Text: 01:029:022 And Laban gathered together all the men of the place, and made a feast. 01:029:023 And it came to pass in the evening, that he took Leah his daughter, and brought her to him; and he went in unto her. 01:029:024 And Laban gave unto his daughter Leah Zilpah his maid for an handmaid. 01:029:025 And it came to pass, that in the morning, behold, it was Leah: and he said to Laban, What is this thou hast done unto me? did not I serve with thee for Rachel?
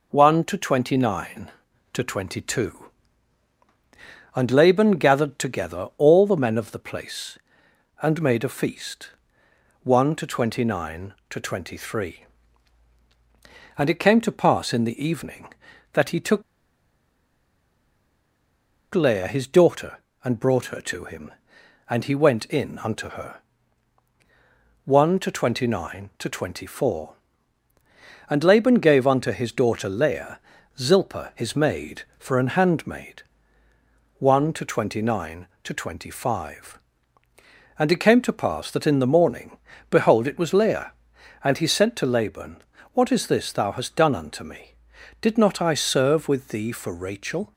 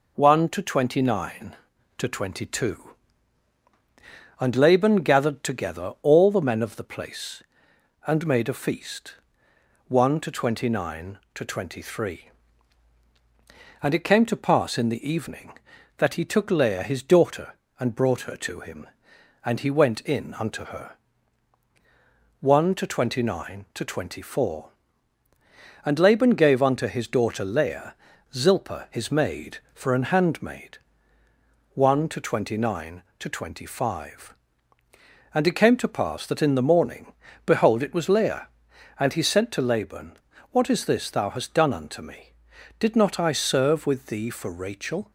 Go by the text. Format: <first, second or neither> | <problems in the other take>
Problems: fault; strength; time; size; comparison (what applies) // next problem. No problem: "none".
second | pauses between "took" and "Leah"; strong; at 16.4 s; 2.5 s long // pauses between "Leah" and "Zilpah"; at 30.3 s; 0.40 s long; also in the second